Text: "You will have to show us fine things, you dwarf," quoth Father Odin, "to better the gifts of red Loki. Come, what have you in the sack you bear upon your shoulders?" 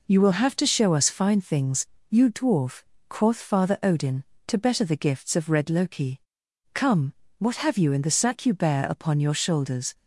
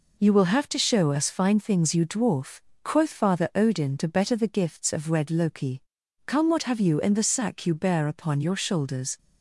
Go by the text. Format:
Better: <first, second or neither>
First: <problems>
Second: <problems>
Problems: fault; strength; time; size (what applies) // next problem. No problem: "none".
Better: neither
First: none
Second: none